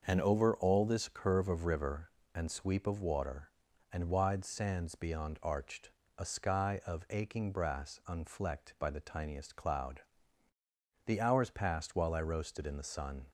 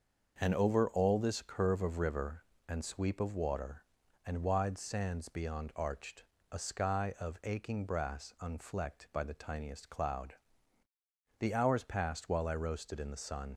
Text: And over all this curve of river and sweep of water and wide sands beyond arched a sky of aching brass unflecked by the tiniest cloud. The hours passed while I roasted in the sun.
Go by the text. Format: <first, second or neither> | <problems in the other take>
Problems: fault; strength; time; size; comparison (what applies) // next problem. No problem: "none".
first | starts louder than the rest; until 1.4 s; 6.5 dB; also in the first // pauses between "arched" and "a"; slight; at 6.2 s; 0.26 s long; slight in the first // leaves "sun" unfinished; at 13.5 s; 85 ms